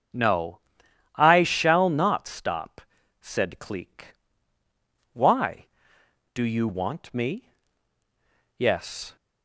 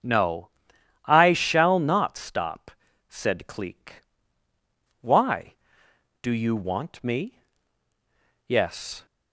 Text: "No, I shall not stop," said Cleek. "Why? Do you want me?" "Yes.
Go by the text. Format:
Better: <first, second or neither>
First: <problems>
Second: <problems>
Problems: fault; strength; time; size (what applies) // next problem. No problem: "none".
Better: neither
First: starts louder than the rest; until 1.7 s; 7 dB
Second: starts louder than the rest; until 1.5 s; 7 dB